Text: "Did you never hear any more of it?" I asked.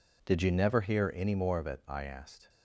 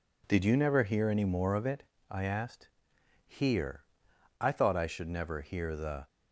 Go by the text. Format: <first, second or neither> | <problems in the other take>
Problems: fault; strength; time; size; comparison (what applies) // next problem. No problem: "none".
first | goes on to say "Hear I thought I should never hear the"; strong; from 3.2 s on; 2.8 s long